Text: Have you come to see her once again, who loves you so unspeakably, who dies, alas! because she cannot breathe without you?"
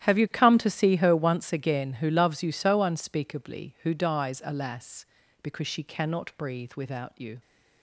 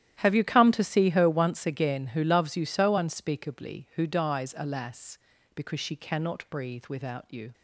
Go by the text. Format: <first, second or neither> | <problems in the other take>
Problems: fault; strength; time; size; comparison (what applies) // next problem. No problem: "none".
neither | starts louder than the rest; strong; the same in both